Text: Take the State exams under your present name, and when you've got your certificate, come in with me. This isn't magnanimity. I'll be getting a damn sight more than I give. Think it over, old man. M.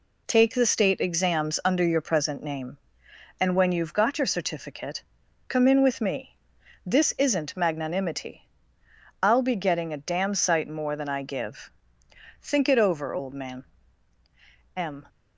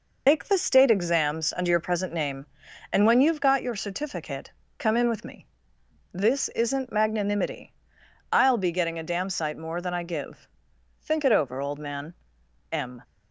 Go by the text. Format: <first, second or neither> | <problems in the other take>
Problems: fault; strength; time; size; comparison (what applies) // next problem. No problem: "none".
first | loses the start of "Take"; at 0.2 s; 95 ms